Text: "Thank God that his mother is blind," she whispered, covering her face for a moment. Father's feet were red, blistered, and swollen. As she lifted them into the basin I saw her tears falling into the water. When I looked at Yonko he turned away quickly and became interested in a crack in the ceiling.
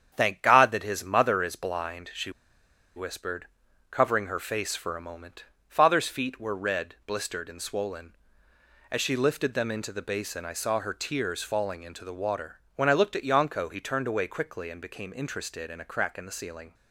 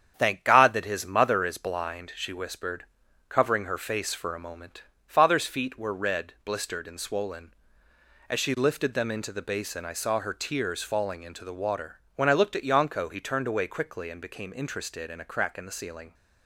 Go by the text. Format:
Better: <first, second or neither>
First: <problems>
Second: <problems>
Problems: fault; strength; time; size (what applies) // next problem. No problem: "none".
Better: second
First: starts louder than the rest; strong; until 1.1 s; 8 dB // pauses between "she" and "whispered"; noticeable; at 2.3 s; 0.65 s long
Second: starts louder than the rest; strong; until 1.1 s; 8 dB